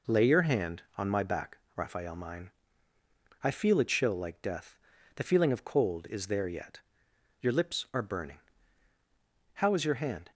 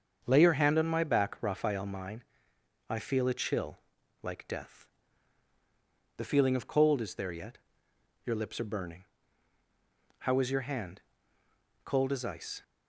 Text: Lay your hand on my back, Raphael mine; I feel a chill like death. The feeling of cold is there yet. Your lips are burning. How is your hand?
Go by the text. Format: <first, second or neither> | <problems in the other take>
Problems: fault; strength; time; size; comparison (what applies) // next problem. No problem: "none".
first | starts louder than the rest; until 1.2 s; 7 dB // pauses between "chill" and "like"; at 3.7 s; 0.44 s long // goes on to say "Cold as ice"; noticeable; from 11.8 s on; 0.80 s long